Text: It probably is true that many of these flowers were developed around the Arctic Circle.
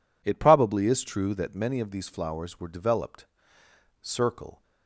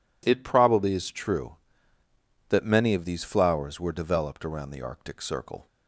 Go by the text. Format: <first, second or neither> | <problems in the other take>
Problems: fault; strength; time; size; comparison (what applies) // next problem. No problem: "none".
second | skips "around the Arctic"; at 3.6 s